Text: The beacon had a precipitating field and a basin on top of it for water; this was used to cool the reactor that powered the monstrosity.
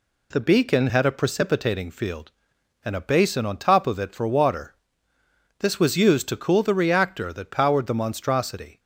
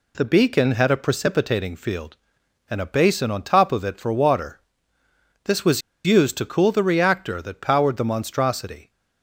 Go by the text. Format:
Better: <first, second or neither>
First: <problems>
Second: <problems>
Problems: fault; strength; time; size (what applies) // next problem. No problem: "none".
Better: first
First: none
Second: pauses between "was" and "used"; slight; at 5.8 s; 0.24 s long